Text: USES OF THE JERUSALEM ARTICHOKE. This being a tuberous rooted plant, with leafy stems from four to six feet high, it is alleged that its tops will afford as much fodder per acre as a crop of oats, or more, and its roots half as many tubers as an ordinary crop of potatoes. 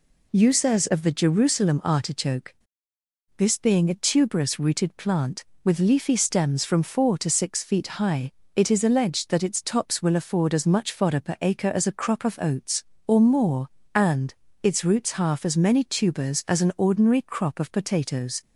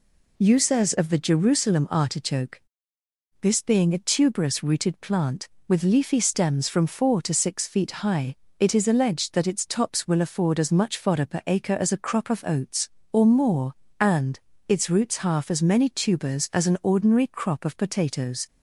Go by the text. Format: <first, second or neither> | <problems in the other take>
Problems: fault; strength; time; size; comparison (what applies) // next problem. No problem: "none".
neither | pauses between "and" and "its"; slight; the same in both